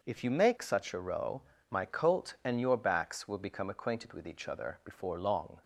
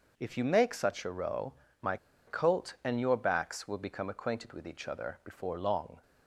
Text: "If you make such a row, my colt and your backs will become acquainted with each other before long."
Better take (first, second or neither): first